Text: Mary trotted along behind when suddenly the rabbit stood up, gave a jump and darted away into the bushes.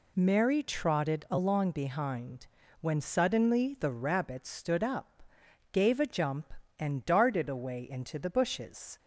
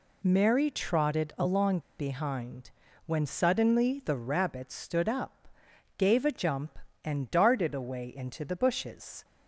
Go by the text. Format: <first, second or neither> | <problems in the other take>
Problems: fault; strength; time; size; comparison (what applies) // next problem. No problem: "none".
first | pauses between "along" and "behind"; slight; at 1.7 s; 0.18 s long // pauses between "behind" and "when"; slight; at 2.6 s; 0.36 s long; slight in the first